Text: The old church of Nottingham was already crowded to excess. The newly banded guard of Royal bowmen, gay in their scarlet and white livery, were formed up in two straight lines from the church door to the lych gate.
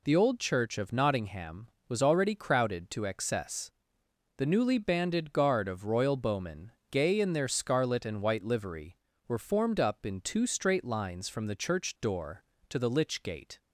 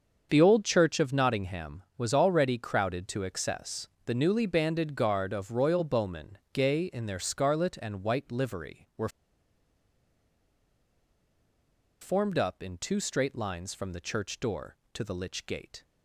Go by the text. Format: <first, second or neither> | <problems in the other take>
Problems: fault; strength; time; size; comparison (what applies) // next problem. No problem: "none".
first | starts louder than the rest; until 1.3 s; 7 dB // pauses between "were" and "formed"; strong; at 9.0 s; 2.9 s long